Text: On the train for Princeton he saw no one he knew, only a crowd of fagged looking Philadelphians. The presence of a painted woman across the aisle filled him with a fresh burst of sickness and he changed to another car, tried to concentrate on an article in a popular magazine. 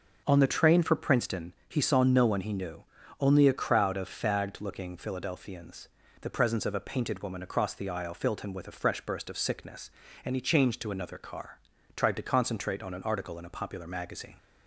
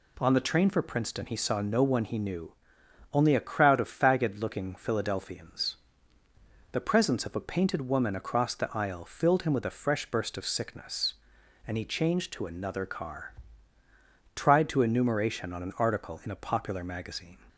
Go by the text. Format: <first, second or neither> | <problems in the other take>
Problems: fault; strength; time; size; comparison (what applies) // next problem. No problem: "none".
first | says "enumeration" for "concentrate"; at 14.8 s